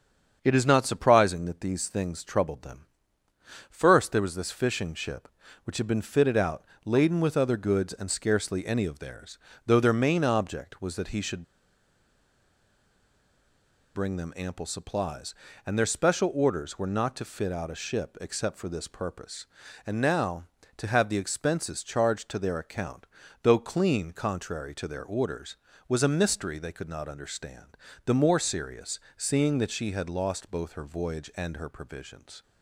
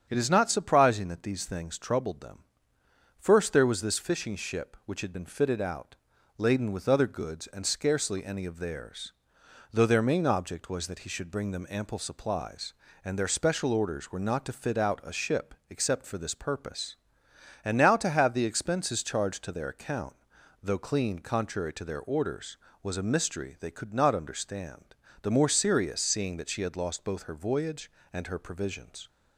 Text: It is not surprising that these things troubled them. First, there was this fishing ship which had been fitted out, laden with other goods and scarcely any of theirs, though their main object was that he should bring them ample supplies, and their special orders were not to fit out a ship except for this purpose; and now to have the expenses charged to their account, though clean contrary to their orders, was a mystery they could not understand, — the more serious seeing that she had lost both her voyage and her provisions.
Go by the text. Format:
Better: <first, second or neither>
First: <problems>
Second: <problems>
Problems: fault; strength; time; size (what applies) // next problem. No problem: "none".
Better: second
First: starts louder than the rest; strong; until 1.4 s; 7.5 dB // pauses between "should" and "bring"; strong; at 11.4 s; 2.5 s long // pauses between "serious" and "seeing"; slight; at 28.9 s; 0.18 s long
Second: starts louder than the rest; strong; until 1.1 s; 8 dB